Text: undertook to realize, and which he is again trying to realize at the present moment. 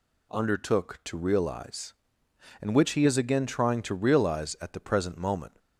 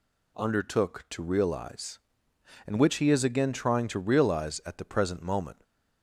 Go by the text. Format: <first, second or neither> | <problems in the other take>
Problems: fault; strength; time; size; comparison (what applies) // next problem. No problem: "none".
neither | none